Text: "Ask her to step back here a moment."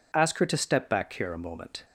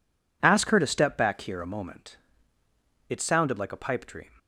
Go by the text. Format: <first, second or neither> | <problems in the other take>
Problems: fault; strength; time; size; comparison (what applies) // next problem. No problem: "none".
first | goes on to say "It sounded like a pipe dream"; noticeable; from 3.0 s on; 1.2 s long